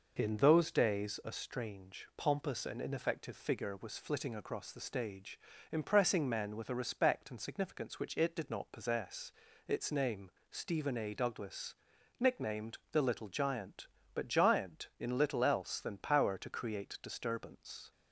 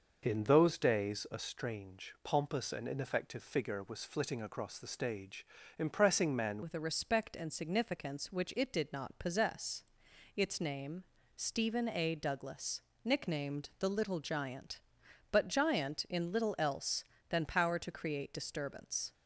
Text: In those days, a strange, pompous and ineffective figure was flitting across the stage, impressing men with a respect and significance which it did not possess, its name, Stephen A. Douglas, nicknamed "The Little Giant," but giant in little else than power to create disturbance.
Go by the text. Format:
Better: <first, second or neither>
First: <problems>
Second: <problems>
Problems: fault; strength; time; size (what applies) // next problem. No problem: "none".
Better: first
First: none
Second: changes voice at "with"; from 6.6 s on; 12.5 s long